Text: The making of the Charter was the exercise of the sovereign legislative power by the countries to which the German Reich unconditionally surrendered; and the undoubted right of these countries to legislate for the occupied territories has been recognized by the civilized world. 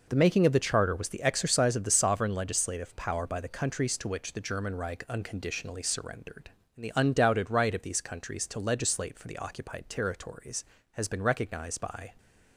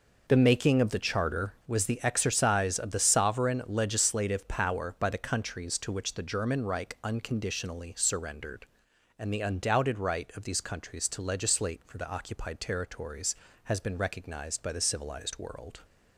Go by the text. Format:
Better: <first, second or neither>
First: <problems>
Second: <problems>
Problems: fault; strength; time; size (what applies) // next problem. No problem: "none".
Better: second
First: stops before "the civilized world"; at 12.1 s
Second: none